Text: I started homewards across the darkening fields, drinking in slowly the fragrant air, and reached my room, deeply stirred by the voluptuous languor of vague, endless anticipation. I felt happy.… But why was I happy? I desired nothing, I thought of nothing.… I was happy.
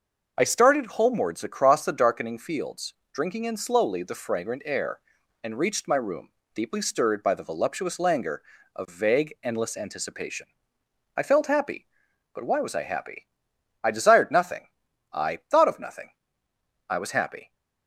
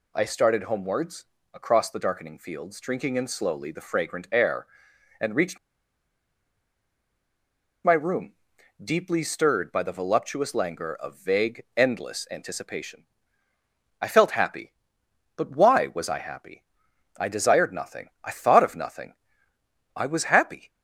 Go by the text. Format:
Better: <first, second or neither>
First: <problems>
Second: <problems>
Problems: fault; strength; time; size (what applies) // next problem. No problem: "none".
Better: first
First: none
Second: pauses between "homewards" and "across"; slight; at 1.2 s; 0.32 s long // pauses between "reached" and "my"; strong; at 5.5 s; 2.2 s long